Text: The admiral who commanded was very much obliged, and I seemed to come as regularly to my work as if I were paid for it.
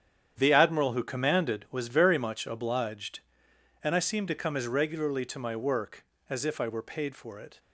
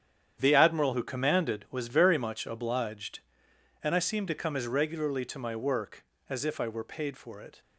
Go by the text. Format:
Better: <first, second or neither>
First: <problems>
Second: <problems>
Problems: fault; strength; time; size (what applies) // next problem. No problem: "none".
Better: neither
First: starts louder than the rest; strong; until 1.3 s; 9 dB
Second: starts louder than the rest; strong; until 1.4 s; 9 dB